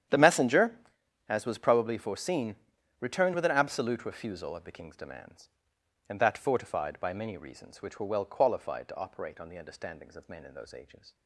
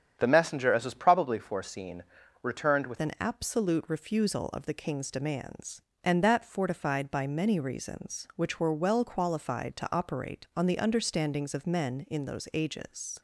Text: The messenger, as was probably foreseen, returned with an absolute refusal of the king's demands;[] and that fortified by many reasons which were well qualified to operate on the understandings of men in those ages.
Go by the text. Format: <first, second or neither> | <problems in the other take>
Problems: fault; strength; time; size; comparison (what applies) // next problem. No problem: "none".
first | starts louder than the rest; strong; until 1.2 s; 8.5 dB; strong in the first // changes voice at "an"; from 2.9 s on; 10.3 s long